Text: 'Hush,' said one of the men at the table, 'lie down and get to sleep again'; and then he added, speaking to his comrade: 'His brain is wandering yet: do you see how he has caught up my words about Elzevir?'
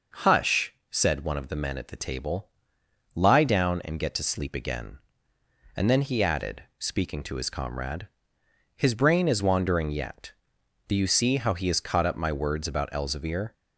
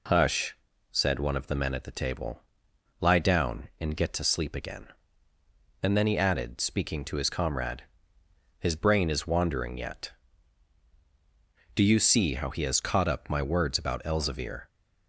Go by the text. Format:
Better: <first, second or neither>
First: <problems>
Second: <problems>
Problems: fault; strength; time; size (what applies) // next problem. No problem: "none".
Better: neither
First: none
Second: none